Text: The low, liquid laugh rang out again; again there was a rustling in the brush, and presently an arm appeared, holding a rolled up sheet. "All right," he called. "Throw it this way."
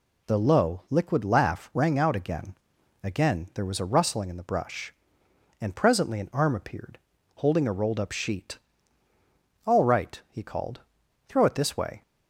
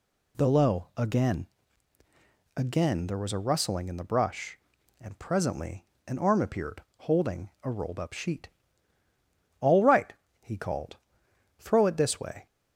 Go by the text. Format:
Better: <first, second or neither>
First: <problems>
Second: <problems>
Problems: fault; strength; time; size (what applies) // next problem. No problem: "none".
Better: first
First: none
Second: skips "liquid laugh rang out"; at 0.9 s // pauses between "presently" and "an"; slight; at 5.8 s; 0.20 s long